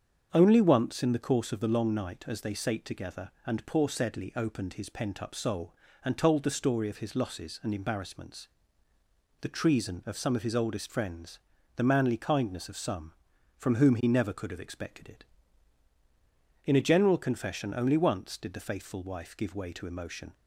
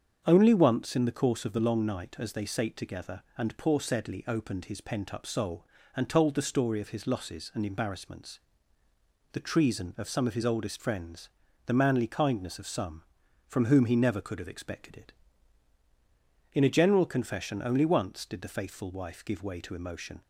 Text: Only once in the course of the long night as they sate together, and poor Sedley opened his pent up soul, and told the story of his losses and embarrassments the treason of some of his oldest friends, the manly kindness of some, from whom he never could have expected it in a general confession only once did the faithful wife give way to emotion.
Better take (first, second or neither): neither